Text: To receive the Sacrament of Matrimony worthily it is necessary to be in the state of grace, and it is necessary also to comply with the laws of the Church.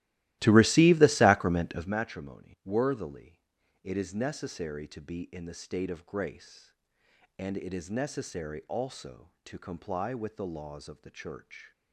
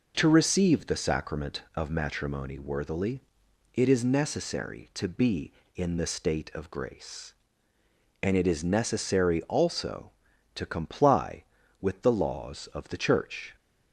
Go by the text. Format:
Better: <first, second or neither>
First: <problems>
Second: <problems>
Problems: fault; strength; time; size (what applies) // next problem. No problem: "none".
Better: second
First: starts louder than the rest; strong; until 1.9 s; 16.5 dB // pauses between "worthily" and "it"; at 3.3 s; 0.42 s long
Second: pauses between "worthily" and "it"; noticeable; at 3.2 s; 0.50 s long